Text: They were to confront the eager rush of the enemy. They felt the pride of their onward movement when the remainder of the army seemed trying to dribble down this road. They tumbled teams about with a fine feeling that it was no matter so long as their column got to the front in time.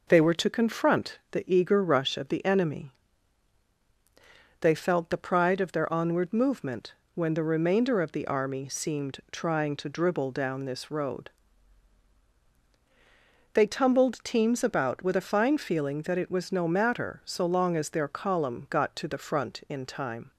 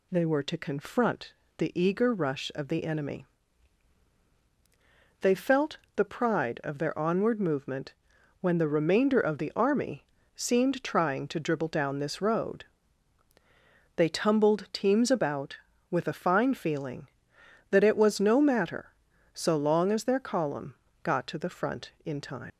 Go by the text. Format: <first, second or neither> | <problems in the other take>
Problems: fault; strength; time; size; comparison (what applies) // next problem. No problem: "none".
first | pauses between "confront" and "the"; slight; at 1.3 s; 0.24 s long // pauses between "felt" and "the"; slight; at 5.7 s; 0.18 s long // pauses between "movement" and "when"; noticeable; at 7.9 s; 0.48 s long; slight in the first // pauses between "army" and "seemed"; slight; at 10.0 s; 0.32 s long // pauses between "column" and "got"; slight; at 20.7 s; 0.28 s long // leaves "time" unfinished; at 22.5 s; 105 ms